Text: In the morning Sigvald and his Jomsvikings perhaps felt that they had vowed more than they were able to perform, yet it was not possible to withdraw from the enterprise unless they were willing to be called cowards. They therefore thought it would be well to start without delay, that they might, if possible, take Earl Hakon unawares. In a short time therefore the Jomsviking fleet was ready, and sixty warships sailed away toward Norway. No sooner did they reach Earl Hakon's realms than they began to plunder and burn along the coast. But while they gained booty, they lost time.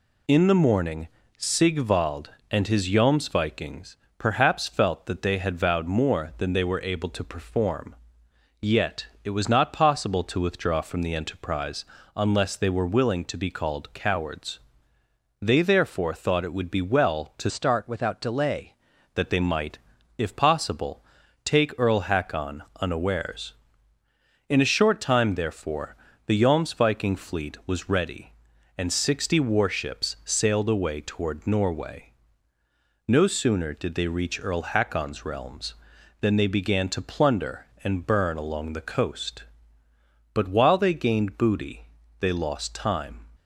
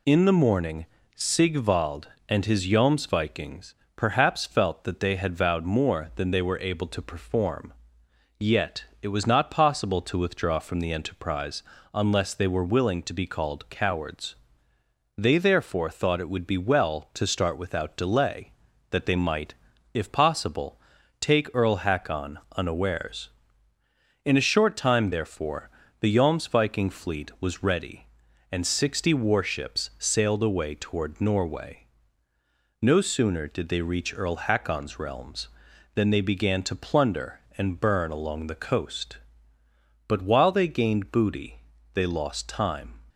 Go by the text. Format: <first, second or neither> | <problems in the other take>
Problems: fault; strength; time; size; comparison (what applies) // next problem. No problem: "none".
second | pauses between "morning" and "Sigvald"; slight; at 1.0 s; 0.28 s long; slight in the second // pauses between "Jomsvikings" and "perhaps"; slight; at 3.9 s; 0.22 s long; slight in the second // pauses between "yet" and "it"; slight; at 9.0 s; 0.18 s long; slight in the second // pauses between "enterprise" and "unless"; slight; at 11.8 s; 0.30 s long; slight in the second // changes voice from "start" to "delay"; from 17.4 to 18.7 s; 1.3 s long // pauses between "Hakon" and "unawares"; slight; at 22.6 s; 0.16 s long; slight in the second // pauses between "therefore" and "the"; slight; at 25.9 s; 0.30 s long; slight in the second